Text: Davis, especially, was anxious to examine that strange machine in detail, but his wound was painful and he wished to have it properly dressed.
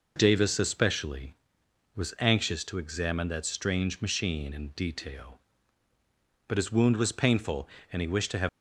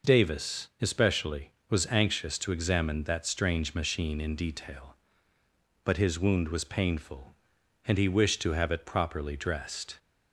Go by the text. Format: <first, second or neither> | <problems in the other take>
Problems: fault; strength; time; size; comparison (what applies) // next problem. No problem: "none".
second | stops before "it properly dressed"; at 8.4 s